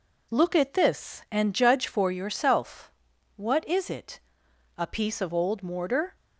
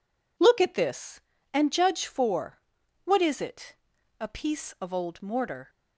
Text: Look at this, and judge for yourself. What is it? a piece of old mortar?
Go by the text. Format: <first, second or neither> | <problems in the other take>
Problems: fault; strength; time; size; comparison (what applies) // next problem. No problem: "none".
first | skips "yourself"; at 2.8 s